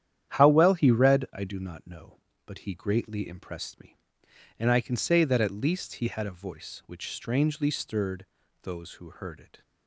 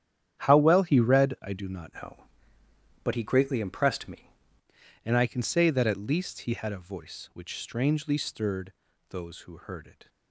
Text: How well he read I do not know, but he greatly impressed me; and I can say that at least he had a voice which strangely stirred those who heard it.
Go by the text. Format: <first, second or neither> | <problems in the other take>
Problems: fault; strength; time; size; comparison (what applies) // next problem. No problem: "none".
first | starts louder than the rest; strong; until 1.4 s; 10 dB; strong in the first // changes voice from "know" to "me"; from 1.9 to 4.3 s; 2.4 s long // pauses between "stirred" and "those"; slight; at 8.7 s; 0.36 s long; slight in the first